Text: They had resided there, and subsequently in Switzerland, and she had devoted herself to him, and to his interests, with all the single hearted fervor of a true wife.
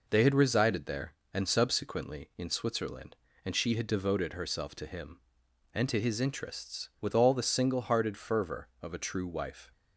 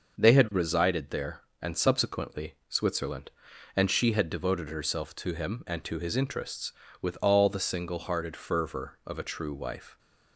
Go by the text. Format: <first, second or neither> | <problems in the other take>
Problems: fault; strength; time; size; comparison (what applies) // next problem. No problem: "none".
first | starts louder than the rest; noticeable; until 1.2 s; 6 dB // skips "in"; at 2.6 s